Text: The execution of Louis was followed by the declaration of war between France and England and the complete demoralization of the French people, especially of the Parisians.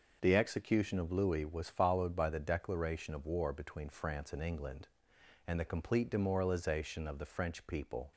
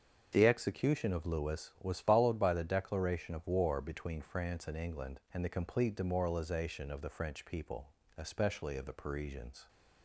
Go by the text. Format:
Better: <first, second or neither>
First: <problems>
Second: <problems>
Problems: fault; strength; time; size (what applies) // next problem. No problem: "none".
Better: second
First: starts louder than the rest; noticeable; until 1.2 s; 6 dB // stops before "especially of the Parisians"; at 8.1 s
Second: starts louder than the rest; until 1.3 s; 7 dB